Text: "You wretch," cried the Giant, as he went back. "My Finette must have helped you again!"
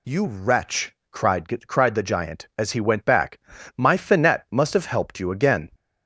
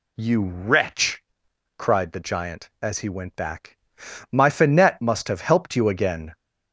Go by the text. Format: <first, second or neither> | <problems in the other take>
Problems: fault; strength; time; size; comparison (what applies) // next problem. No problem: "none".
second | says "cried" twice; at 1.6 s